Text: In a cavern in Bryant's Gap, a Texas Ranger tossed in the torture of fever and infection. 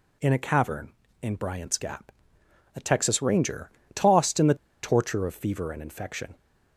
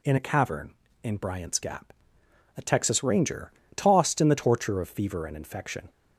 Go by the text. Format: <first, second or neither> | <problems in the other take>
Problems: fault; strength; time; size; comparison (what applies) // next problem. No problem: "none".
second | pauses between "Ranger" and "tossed"; slight; at 3.7 s; 0.24 s long; slight in the second // pauses between "the" and "torture"; slight; at 4.5 s; 0.28 s long